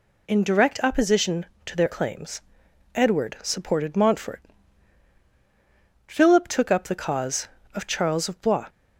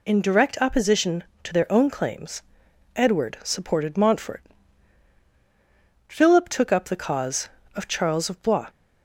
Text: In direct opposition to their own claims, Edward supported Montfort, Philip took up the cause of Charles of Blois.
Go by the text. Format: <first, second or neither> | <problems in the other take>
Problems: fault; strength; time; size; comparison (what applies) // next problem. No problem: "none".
second | skips "own"; at 1.9 s